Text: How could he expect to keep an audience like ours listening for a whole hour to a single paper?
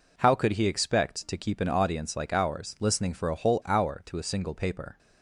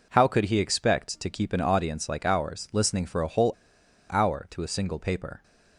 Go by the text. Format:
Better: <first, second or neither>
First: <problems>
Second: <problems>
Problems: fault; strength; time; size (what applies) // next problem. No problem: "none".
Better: first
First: none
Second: pauses between "whole" and "hour"; noticeable; at 3.5 s; 0.58 s long